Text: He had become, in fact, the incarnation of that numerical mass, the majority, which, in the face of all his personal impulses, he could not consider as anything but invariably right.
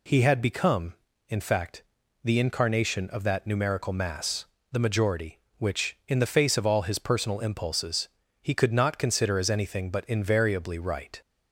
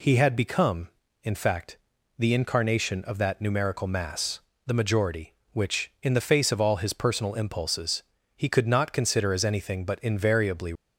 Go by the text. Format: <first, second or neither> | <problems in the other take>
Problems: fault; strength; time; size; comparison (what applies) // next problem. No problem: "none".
first | stops before "right"; at 10.7 s